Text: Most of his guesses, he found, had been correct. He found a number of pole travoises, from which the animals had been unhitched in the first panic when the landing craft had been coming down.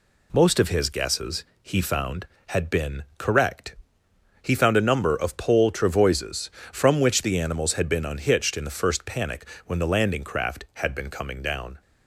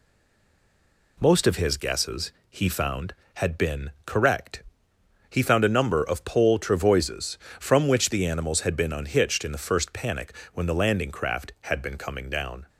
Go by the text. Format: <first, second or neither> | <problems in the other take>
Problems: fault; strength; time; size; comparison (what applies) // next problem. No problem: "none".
first | stays silent before the first word; until 1.1 s; 1.1 s long // pauses between "panic" and "when"; slight; at 10.3 s; 0.22 s long; slight in the first